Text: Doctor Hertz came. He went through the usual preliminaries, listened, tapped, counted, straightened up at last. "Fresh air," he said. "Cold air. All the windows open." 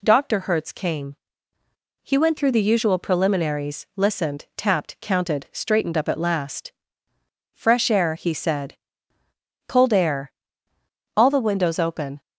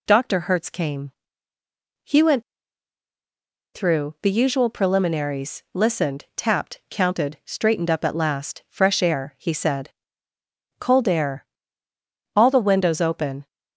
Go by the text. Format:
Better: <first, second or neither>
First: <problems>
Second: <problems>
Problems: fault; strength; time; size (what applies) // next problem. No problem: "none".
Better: first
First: none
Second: pauses between "went" and "through"; strong; at 2.4 s; 1.3 s long